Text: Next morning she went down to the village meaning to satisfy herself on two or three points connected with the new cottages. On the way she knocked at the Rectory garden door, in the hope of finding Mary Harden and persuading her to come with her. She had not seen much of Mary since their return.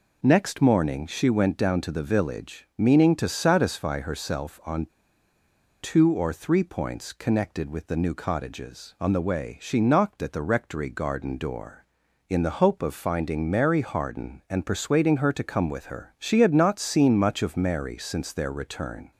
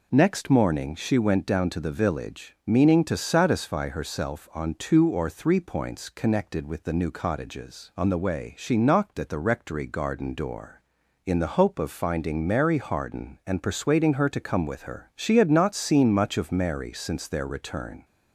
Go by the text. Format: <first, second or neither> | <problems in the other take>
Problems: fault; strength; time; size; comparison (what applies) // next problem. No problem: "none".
second | pauses between "on" and "two"; noticeable; at 4.8 s; 0.94 s long